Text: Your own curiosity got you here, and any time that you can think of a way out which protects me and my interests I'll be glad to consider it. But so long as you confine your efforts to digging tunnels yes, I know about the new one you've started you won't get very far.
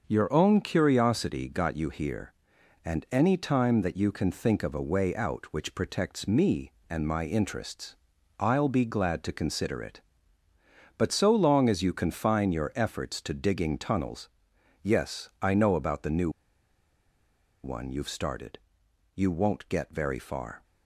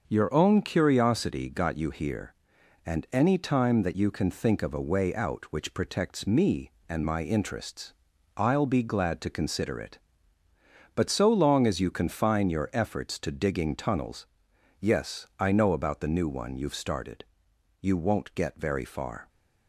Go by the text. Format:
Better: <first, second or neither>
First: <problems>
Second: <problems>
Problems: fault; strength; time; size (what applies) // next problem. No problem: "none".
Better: second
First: starts louder than the rest; until 1.0 s; 6 dB // pauses between "interests" and "I'll"; at 7.9 s; 0.44 s long // pauses between "tunnels" and "yes"; noticeable; at 14.2 s; 0.54 s long // pauses between "new" and "one"; strong; at 16.2 s; 1.3 s long // pauses between "started" and "you"; noticeable; at 18.5 s; 0.58 s long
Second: starts louder than the rest; until 1.0 s; 6 dB // pauses between "interests" and "I'll"; at 7.9 s; 0.44 s long // pauses between "tunnels" and "yes"; noticeable; at 14.2 s; 0.54 s long // pauses between "started" and "you"; noticeable; at 17.2 s; 0.58 s long